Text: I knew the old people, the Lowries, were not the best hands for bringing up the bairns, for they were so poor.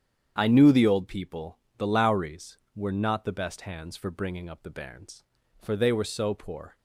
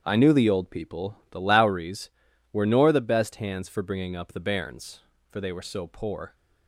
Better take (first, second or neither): first